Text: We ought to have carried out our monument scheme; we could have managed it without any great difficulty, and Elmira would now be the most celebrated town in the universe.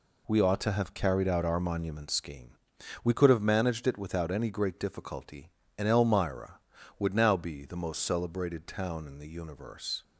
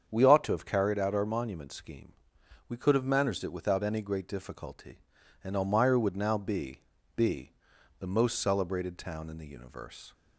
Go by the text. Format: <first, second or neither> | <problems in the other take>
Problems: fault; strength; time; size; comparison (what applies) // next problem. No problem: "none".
first | starts louder than the rest; strong; until 1.0 s; 7.5 dB // says "be" twice; at 7.1 s